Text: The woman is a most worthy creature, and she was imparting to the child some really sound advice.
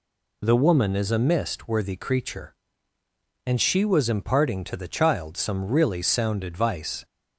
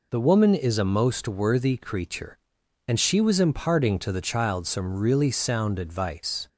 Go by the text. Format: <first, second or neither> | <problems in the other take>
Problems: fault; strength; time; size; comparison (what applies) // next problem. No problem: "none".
second | says "mist" for "most"; at 1.1 s